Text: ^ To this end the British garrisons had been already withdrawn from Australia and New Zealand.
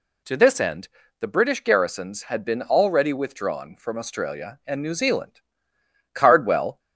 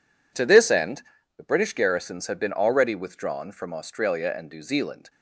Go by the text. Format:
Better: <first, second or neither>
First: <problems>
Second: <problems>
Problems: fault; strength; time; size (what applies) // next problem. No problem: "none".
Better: second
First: pauses between "end" and "the"; slight; at 0.8 s; 0.30 s long // goes on to say "Cardwell"; noticeable; from 6.1 s on; 0.64 s long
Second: pauses between "end" and "the"; slight; at 1.0 s; 0.36 s long